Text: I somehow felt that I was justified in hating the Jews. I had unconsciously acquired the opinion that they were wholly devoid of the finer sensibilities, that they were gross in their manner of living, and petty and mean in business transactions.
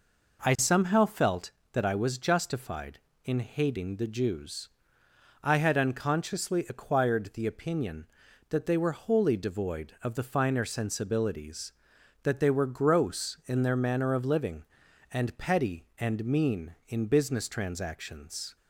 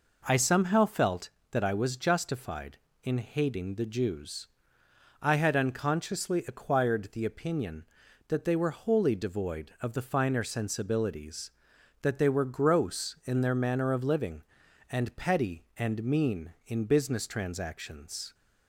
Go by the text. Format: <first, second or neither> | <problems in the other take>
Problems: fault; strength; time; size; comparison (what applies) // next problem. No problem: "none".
neither | none